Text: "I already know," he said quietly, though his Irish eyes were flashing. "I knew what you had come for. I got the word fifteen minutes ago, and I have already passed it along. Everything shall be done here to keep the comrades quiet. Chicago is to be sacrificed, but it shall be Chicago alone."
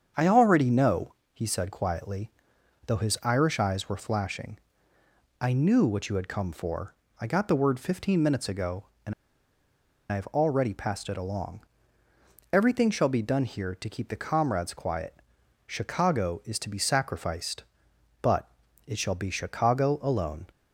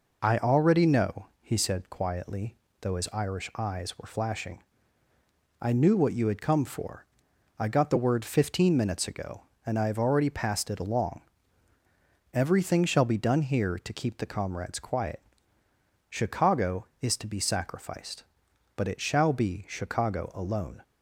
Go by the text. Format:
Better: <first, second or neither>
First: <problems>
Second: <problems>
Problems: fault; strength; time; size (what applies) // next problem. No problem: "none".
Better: second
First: starts louder than the rest; strong; until 1.3 s; 7.5 dB // pauses between "and" and "I"; at 9.1 s; 0.98 s long // pauses between "but" and "it"; slight; at 18.5 s; 0.36 s long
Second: none